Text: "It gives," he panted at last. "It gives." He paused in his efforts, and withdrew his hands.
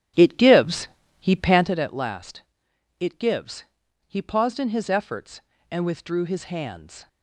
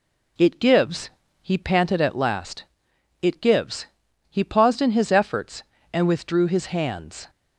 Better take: second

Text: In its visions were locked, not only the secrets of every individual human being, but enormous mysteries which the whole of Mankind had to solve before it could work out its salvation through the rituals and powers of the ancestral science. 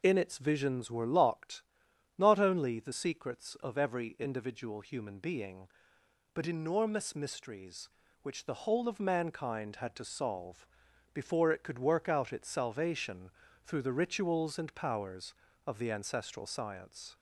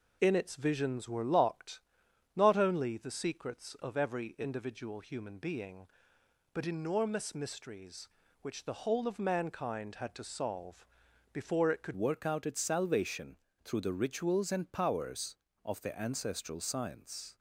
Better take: first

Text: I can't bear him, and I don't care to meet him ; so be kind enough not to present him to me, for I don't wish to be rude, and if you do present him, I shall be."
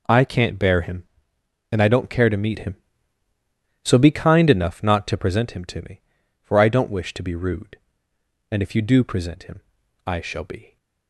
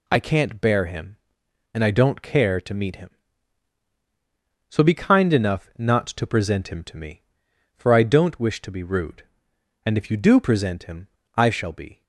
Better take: neither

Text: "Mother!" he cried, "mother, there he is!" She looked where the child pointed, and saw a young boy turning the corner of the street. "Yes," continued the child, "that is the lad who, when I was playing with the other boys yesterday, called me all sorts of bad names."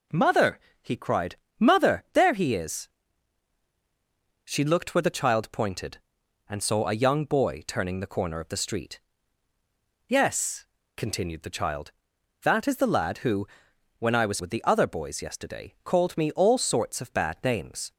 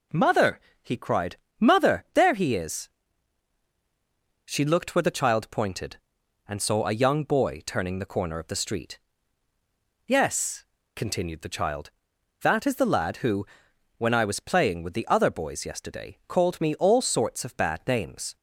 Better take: second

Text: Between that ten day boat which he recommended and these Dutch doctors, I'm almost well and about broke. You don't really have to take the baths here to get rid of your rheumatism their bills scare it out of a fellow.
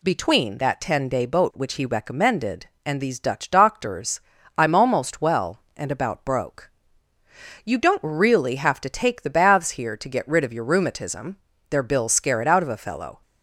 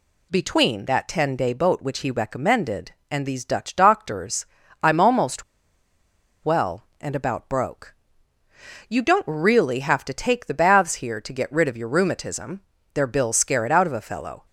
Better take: first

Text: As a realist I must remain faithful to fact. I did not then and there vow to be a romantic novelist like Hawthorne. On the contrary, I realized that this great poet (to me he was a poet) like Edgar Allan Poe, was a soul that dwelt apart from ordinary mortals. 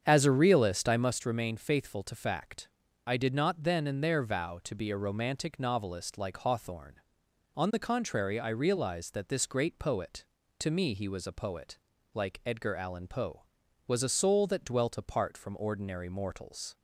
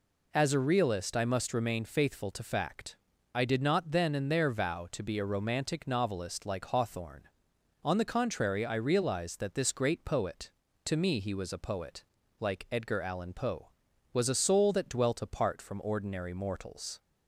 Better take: second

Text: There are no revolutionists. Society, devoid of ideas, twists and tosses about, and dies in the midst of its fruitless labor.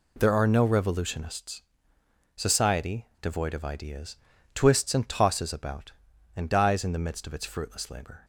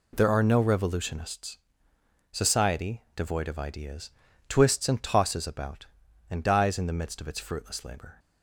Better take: neither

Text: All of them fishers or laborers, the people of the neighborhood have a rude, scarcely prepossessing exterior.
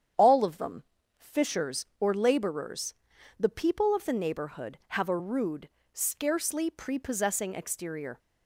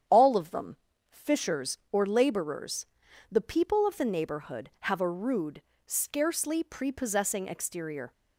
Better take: neither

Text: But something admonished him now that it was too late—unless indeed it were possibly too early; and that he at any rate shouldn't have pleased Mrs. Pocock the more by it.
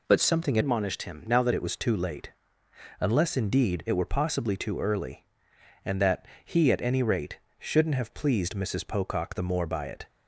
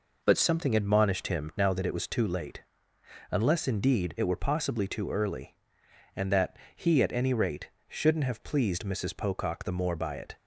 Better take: second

